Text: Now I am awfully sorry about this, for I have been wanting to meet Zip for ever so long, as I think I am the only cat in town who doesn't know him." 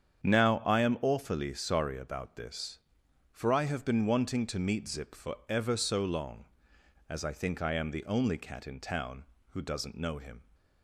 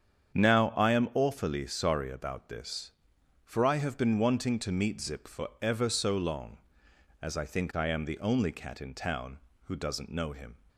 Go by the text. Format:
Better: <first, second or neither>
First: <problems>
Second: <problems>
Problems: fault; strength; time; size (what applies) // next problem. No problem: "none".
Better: neither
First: starts louder than the rest; strong; until 1.2 s; 8 dB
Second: starts louder than the rest; strong; until 1.3 s; 8 dB